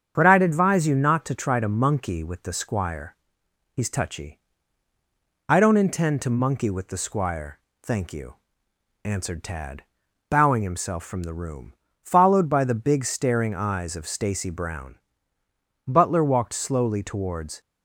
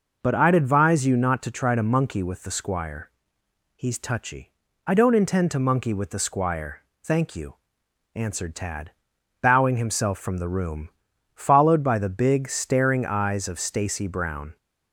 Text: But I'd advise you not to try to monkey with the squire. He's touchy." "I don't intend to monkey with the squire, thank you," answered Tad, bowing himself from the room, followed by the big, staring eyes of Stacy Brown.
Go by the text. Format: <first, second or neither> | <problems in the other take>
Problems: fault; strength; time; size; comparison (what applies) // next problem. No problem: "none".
second | starts louder than the rest; strong; until 1.1 s; 7.5 dB // goes on to say "Butler walked slowly towards"; strong; from 15.8 s on; 1.7 s long